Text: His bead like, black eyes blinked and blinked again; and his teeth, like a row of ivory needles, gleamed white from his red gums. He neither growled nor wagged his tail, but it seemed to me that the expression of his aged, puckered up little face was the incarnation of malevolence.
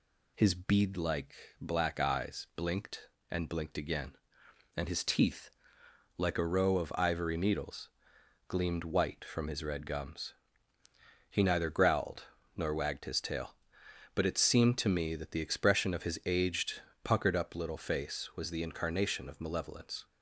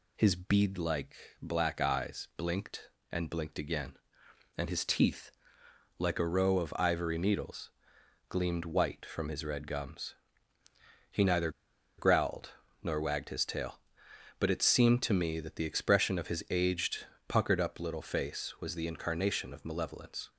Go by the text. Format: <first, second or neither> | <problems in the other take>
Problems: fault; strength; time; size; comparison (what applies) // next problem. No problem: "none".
first | pauses between "neither" and "growled"; noticeable; at 11.4 s; 0.48 s long // pauses between "growled" and "nor"; slight; at 12.5 s; 0.32 s long; slight in the first